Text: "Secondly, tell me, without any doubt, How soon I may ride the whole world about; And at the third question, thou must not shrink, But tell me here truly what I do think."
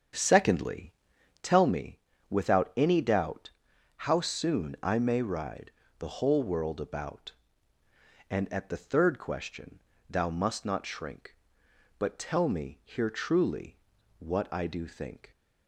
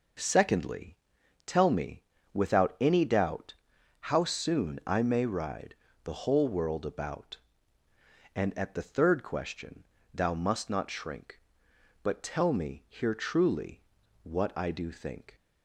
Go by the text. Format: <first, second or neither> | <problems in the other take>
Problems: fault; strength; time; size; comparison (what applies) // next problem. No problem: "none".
second | starts louder than the rest; strong; until 1.7 s; 7.5 dB // pauses between "ride" and "the"; slight; at 5.7 s; 0.28 s long; slight in the second // pauses between "truly" and "what"; at 13.7 s; 0.40 s long; also in the second